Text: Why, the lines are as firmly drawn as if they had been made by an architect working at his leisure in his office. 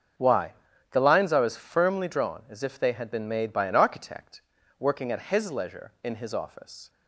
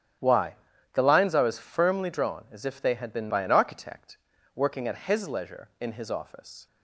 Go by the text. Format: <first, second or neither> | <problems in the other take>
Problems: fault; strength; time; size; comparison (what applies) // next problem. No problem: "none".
first | starts louder than the rest; strong; until 1.5 s; 11 dB; also in the first // skips "made"; at 3.3 s // pauses between "architect" and "working"; at 4.1 s; 0.38 s long; also in the first